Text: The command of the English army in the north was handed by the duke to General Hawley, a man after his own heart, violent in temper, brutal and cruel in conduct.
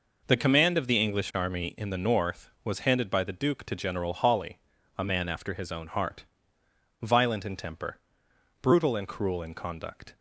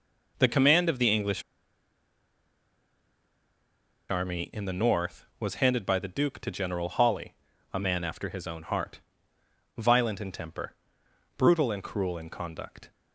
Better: first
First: none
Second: pauses between "English" and "army"; strong; at 1.4 s; 2.6 s long

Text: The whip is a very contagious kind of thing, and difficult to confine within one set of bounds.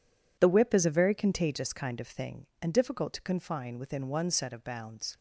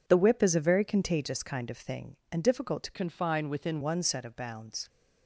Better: first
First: none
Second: changes voice from "confine" to "within"; from 2.9 to 3.8 s; 0.9 s long

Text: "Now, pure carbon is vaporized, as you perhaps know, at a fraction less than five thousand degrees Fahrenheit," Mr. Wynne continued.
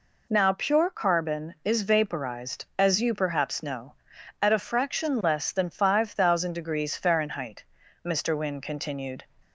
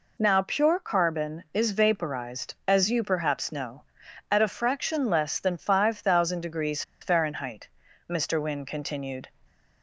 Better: first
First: none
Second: pauses between "degrees" and "Fahrenheit"; slight; at 6.8 s; 0.19 s long

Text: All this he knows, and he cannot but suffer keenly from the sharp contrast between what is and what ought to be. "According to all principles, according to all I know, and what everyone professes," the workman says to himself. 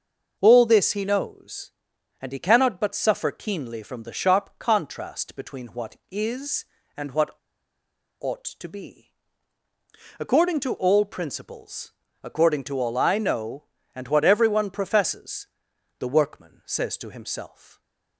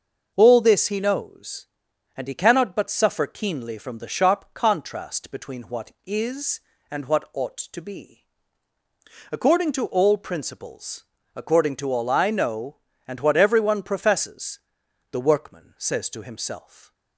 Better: second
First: starts louder than the rest; noticeable; until 1.4 s; 6 dB // pauses between "what" and "ought"; noticeable; at 7.3 s; 0.87 s long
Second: starts louder than the rest; noticeable; until 1.3 s; 6 dB

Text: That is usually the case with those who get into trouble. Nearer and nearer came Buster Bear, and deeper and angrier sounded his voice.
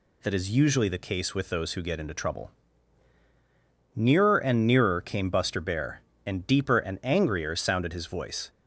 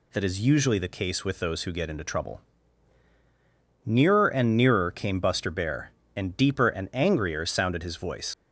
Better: first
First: none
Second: leaves "voice" unfinished; at 8.3 s; 60 ms

